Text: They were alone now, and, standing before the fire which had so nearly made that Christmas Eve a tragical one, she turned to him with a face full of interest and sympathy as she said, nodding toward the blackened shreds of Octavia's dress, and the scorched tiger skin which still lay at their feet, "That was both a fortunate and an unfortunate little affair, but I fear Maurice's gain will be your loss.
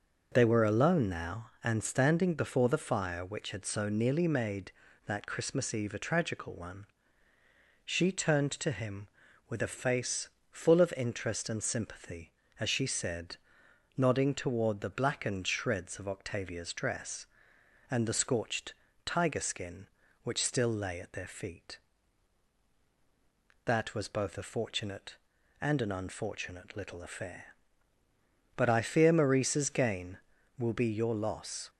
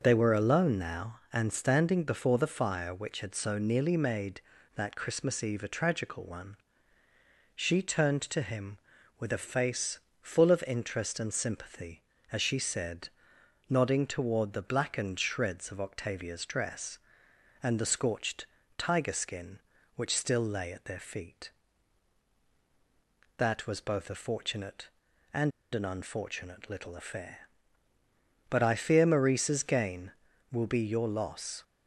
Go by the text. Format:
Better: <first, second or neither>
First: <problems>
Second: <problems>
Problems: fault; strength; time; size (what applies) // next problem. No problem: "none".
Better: first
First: pauses between "face" and "full"; slight; at 10.2 s; 0.20 s long // pauses between "scorched" and "tiger"; slight; at 18.7 s; 0.32 s long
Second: pauses between "face" and "full"; slight; at 9.9 s; 0.20 s long // pauses between "scorched" and "tiger"; slight; at 18.4 s; 0.32 s long // pauses between "and" and "an"; slight; at 25.5 s; 0.22 s long